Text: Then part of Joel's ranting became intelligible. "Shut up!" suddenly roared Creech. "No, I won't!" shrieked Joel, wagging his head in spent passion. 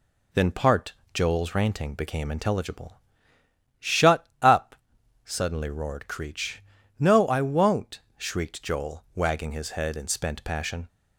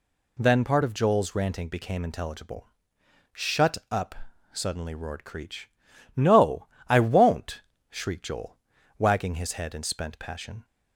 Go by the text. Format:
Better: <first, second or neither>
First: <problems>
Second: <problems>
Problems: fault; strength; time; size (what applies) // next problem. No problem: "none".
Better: second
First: skips "of"; at 1.0 s // pauses between "Shut" and "up"; slight; at 4.2 s; 0.15 s long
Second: none